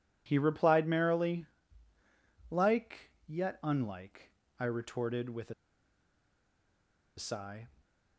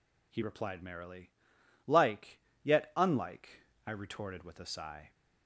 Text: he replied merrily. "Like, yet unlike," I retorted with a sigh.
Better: second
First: pauses between "a" and "sigh"; strong; at 5.5 s; 1.6 s long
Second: none

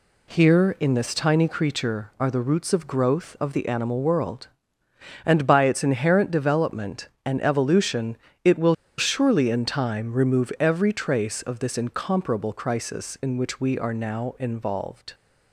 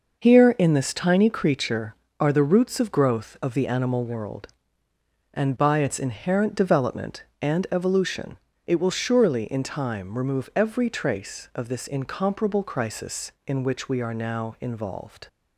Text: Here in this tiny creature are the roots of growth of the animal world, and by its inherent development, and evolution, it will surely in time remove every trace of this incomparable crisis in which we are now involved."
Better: second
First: pauses between "will" and "surely"; slight; at 8.7 s; 0.23 s long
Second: none

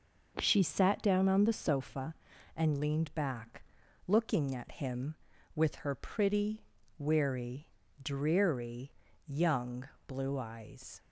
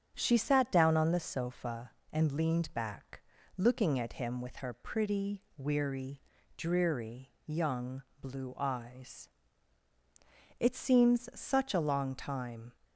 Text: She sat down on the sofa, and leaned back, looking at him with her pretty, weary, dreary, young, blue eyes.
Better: first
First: none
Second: starts louder than the rest; strong; until 1.1 s; 8 dB // goes on to say "It seems such a long time"; strong; from 10.5 s on; 2.1 s long

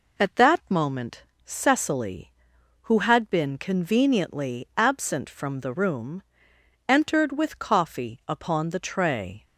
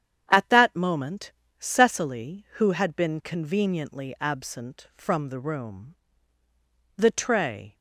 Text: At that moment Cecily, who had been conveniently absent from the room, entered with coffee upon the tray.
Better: first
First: pauses between "moment" and "Cecily"; slight; at 1.2 s; 0.20 s long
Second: starts louder than the rest; strong; until 1.3 s; 9 dB // pauses between "moment" and "Cecily"; slight; at 1.3 s; 0.26 s long // skips "entered with coffee upon"; at 6.4 s

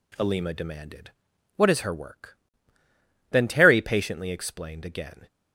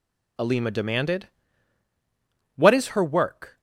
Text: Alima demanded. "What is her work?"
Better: second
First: goes on to say "Then Terry patiently explained again"; strong; from 3.3 s on; 1.9 s long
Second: none

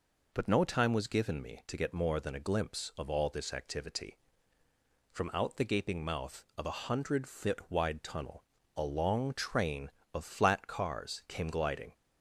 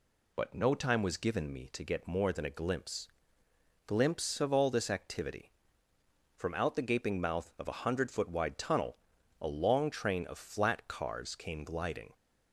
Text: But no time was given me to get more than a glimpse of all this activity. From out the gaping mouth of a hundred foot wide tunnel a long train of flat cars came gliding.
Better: first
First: pauses between "tunnel" and "a"; slight; at 8.4 s; 0.32 s long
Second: says "glimpse" twice; at 3.8 s // pauses between "tunnel" and "a"; at 8.9 s; 0.44 s long

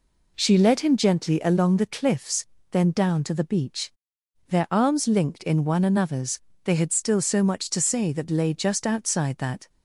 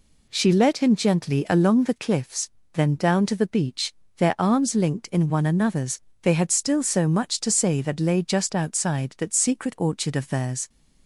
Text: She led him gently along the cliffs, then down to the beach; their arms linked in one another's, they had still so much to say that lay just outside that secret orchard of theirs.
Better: second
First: stops before "secret orchard of theirs"; at 9.6 s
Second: none

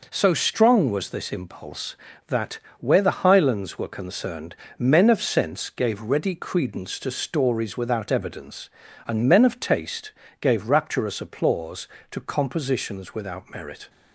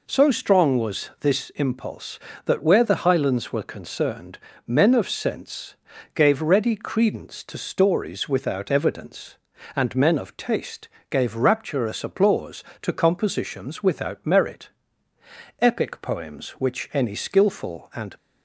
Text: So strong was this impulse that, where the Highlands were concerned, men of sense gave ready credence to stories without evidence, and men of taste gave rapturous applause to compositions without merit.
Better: first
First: pauses between "taste" and "gave"; slight; at 10.1 s; 0.28 s long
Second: pauses between "sense" and "gave"; at 5.7 s; 0.40 s long // pauses between "taste" and "gave"; slight; at 10.8 s; 0.24 s long // goes on to say "Epic poems which any skilful and"; strong; from 15.5 s on; 2.5 s long

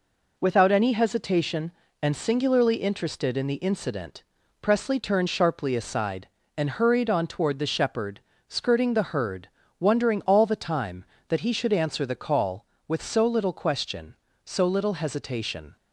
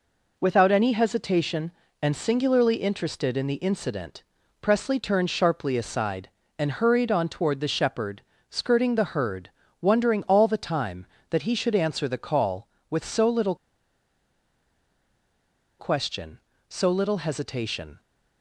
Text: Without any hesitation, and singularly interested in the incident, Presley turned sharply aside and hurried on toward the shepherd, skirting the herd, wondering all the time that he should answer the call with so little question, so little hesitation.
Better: first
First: none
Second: pauses between "little" and "question"; strong; at 13.5 s; 2.2 s long

